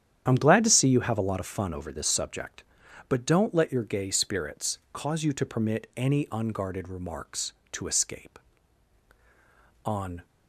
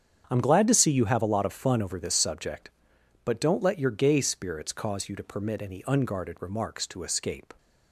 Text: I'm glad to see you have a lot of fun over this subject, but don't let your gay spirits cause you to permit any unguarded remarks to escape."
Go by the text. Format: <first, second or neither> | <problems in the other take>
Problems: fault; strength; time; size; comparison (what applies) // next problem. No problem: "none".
second | starts louder than the rest; strong; until 1.2 s; 10 dB; strong in the second // goes on to say "On"; slight; from 9.8 s on; 0.42 s long